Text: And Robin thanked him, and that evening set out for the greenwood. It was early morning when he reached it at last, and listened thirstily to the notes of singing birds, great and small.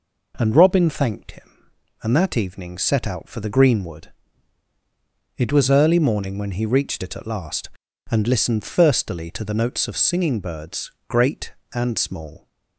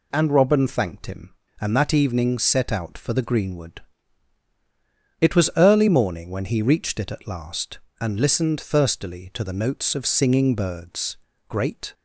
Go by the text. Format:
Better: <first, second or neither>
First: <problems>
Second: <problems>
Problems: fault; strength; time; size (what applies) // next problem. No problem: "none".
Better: first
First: none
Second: stops before "and small"; at 11.9 s